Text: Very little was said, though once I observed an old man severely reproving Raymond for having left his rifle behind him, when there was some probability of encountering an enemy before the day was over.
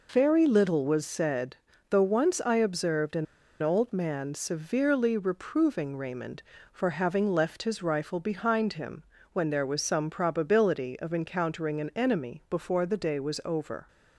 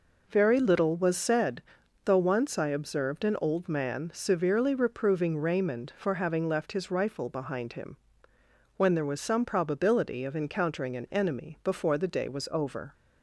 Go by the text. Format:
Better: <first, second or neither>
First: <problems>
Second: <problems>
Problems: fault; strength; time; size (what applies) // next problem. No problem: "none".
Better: second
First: pauses between "an" and "old"; at 3.2 s; 0.37 s long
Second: none